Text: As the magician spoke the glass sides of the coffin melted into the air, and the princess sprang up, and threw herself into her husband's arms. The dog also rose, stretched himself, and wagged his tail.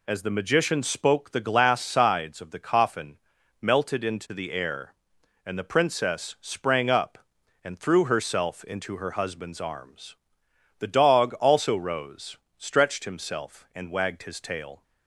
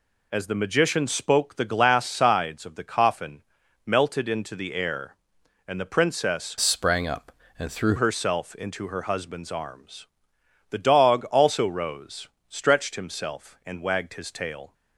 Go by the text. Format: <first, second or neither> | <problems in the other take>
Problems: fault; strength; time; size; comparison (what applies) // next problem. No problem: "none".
first | pauses between "coffin" and "melted"; at 3.4 s; 0.44 s long; also in the first // changes voice from "sprang" to "threw"; from 6.6 to 7.9 s; 1.3 s long